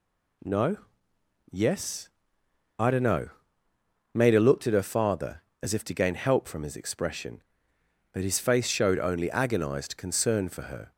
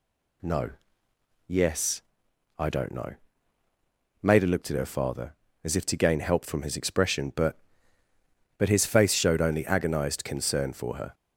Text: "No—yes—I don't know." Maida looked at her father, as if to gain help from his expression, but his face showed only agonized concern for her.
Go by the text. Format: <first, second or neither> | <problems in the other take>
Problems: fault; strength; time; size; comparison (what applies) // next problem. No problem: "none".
first | says "but" twice; at 8.5 s